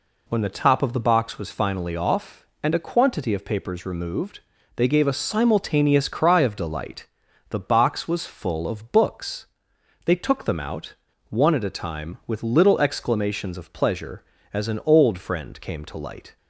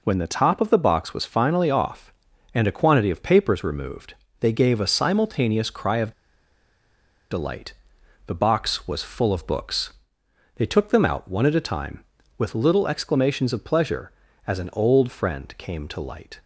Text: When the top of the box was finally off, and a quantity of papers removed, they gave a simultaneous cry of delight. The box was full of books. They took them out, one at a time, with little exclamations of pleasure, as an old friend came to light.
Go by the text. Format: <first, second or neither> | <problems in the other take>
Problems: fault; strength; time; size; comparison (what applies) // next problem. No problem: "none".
first | pauses between "of" and "delight"; at 6.1 s; 1.1 s long